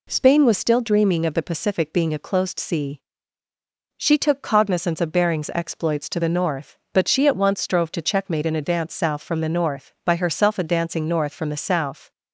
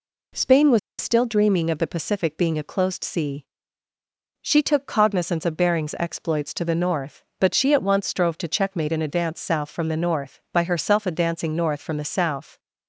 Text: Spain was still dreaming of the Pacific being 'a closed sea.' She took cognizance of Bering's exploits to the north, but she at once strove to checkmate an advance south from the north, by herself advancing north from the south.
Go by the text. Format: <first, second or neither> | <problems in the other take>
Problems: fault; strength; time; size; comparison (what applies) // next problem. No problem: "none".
first | pauses between "was" and "still"; slight; at 0.7 s; 0.21 s long